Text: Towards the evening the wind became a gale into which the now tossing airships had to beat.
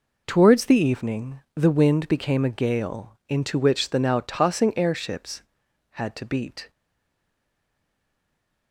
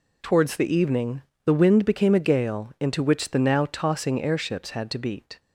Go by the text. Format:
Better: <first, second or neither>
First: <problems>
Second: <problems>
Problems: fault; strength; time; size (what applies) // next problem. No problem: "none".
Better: second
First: pauses between "evening" and "the"; slight; at 1.3 s; 0.16 s long // stays silent after the last word; noticeable; from 6.6 s on; 2.1 s long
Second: pauses between "evening" and "the"; slight; at 1.2 s; 0.22 s long